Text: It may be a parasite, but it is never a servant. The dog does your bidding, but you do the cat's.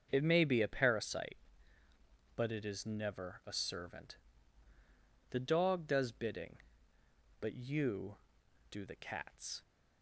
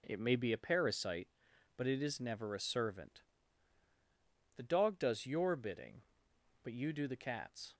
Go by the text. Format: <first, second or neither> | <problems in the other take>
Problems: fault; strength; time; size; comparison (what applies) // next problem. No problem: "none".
second | starts louder than the rest; until 1.1 s; 6.5 dB // skips "your"; at 6.1 s